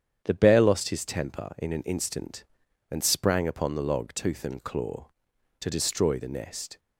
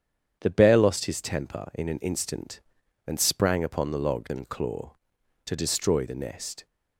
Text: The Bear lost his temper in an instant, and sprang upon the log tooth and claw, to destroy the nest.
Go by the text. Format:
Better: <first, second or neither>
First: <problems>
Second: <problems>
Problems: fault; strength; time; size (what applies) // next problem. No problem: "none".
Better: first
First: starts louder than the rest; strong; until 1.2 s; 8.5 dB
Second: starts louder than the rest; strong; until 1.4 s; 8.5 dB // skips "tooth"; at 4.2 s